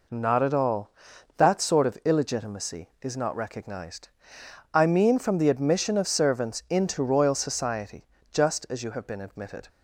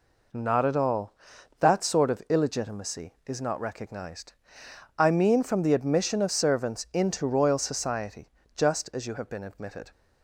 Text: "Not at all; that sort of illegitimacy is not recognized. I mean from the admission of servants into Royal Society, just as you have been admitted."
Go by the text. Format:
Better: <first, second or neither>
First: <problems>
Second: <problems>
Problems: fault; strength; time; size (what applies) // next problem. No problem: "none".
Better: neither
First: none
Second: none